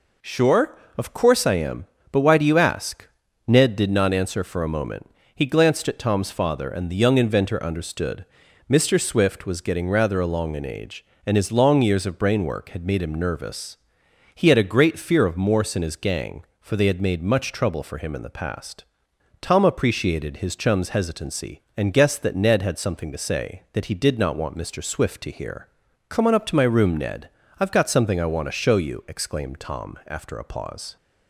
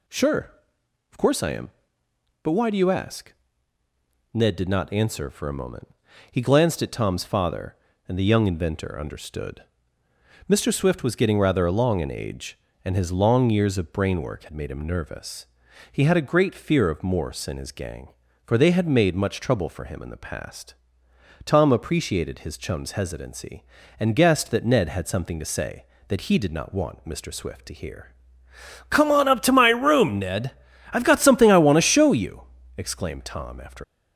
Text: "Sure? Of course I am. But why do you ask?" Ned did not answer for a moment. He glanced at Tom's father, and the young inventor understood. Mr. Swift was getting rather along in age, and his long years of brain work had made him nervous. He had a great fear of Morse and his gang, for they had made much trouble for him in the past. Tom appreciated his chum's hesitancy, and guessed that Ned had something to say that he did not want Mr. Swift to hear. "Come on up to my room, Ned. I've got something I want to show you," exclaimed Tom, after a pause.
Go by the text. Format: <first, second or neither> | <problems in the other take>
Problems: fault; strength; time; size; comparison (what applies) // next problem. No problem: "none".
first | stops before "a pause"; at 33.8 s